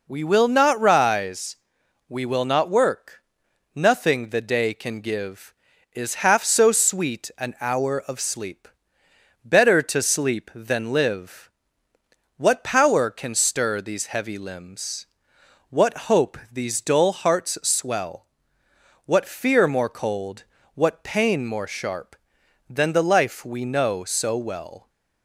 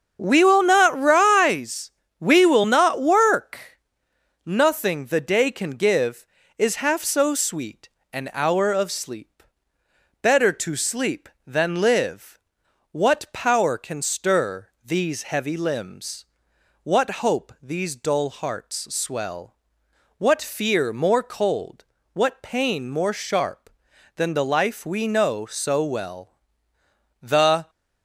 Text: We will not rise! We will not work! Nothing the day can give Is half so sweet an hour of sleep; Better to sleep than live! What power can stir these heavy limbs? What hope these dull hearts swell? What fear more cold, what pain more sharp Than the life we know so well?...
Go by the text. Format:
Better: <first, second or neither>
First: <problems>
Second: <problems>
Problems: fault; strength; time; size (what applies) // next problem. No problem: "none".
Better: first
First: none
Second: starts louder than the rest; until 1.2 s; 7 dB // pauses between "sweet" and "an"; slight; at 7.8 s; 0.24 s long // pauses between "stir" and "these"; slight; at 14.6 s; 0.16 s long // goes on to say "The"; slight; from 27.2 s on; 0.48 s long